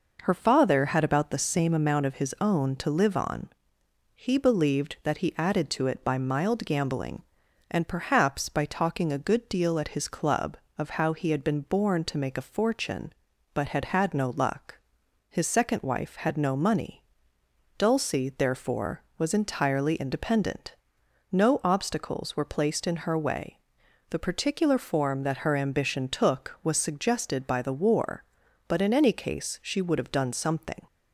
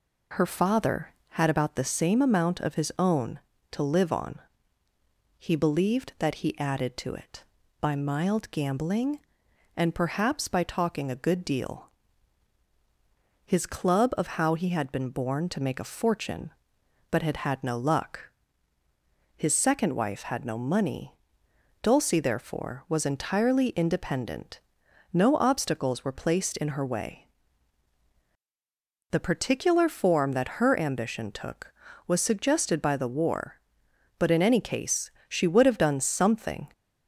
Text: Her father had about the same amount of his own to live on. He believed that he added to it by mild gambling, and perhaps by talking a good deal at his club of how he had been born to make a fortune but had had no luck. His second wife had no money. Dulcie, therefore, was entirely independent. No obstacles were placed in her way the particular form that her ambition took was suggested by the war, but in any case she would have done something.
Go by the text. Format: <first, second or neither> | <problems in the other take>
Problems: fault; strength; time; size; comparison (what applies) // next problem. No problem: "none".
first | skips "at"; at 12.6 s // pauses between "way" and "the"; strong; at 27.2 s; 1.8 s long; noticeable in the first // pauses between "case" and "she"; slight; at 35.0 s; 0.18 s long